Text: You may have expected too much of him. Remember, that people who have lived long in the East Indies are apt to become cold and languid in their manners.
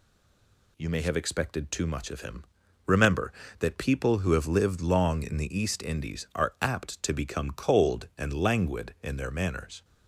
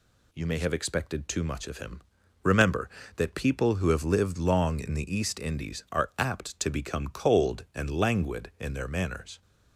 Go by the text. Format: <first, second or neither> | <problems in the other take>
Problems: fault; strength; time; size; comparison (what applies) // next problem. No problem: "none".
second | stays silent before the first word; slight; until 0.7 s; 0.7 s long